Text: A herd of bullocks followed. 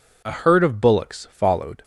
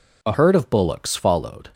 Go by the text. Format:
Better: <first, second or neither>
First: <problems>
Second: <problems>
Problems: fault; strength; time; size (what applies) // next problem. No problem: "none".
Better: first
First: none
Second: changes voice at "herd"; from 0.3 s on; 1.3 s long